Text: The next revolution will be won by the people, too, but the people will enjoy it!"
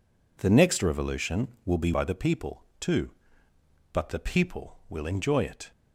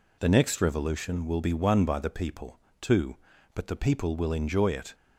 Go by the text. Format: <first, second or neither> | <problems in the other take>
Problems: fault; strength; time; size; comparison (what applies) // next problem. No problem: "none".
second | skips "won"; at 1.9 s